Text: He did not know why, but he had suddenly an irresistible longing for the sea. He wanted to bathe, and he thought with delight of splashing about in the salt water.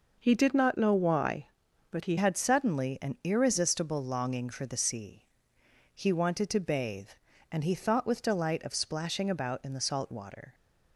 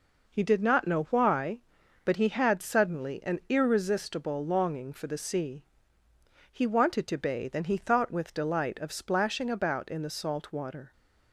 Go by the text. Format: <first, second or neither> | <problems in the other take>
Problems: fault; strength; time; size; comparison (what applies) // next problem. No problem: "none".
second | changes voice at "had"; from 2.1 s on; 8.4 s long